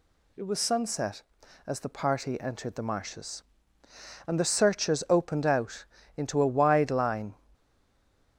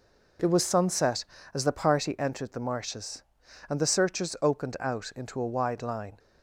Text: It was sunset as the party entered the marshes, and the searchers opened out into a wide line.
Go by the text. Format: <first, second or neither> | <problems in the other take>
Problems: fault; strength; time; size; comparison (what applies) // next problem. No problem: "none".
second | pauses between "out" and "into"; slight; at 5.8 s; 0.32 s long // stays silent after the last word; slight; from 7.5 s on; 0.8 s long